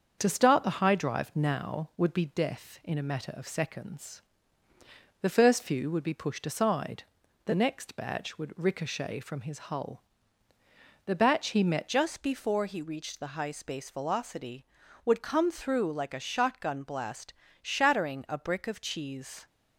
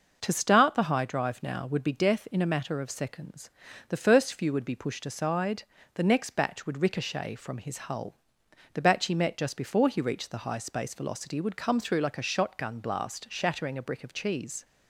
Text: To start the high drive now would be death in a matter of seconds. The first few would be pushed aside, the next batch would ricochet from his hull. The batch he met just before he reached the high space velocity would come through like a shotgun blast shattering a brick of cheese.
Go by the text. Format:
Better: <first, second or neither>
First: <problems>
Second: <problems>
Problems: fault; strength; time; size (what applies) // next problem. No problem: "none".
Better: second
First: starts louder than the rest; until 1.2 s; 7 dB // changes voice at "just"; from 11.8 s on; 7.6 s long // pauses between "blast" and "shattering"; slight; at 17.3 s; 0.26 s long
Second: none